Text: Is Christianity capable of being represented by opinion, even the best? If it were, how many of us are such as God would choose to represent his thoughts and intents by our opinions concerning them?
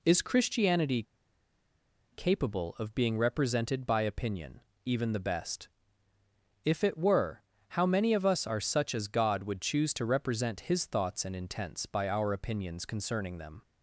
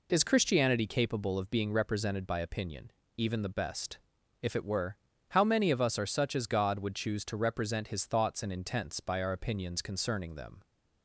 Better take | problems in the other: second | pauses between "Christianity" and "capable"; at 1.0 s; 1.0 s long

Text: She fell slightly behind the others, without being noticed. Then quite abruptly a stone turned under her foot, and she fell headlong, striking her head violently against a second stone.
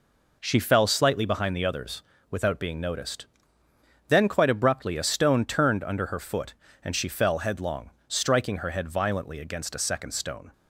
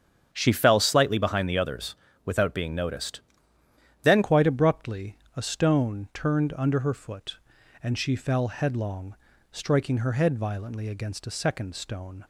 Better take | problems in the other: first | starts louder than the rest; strong; until 1.3 s; 8 dB // changes voice at "quite"; from 4.2 s on; 8.0 s long // pauses between "abruptly" and "a"; slight; at 5.1 s; 0.20 s long

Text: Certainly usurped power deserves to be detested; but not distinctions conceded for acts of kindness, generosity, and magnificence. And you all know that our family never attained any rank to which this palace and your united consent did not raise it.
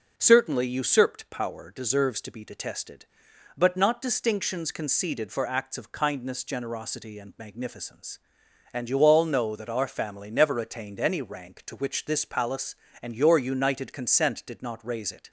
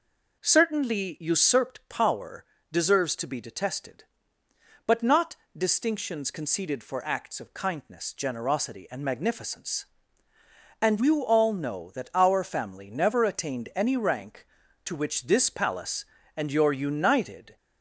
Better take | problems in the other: first | pauses between "power" and "deserves"; slight; at 2.4 s; 0.26 s long // pauses between "not" and "distinctions"; slight; at 5.3 s; 0.22 s long // stops before "consent did not raise it"; at 17.5 s

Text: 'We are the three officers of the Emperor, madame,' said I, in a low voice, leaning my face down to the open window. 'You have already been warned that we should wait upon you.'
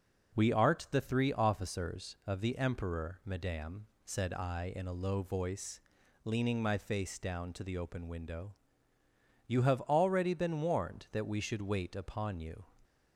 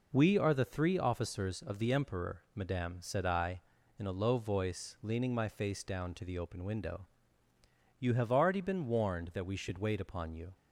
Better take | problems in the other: second | says "art" for "are"; at 0.5 s

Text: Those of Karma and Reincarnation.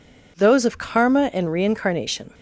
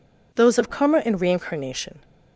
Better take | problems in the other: neither | none

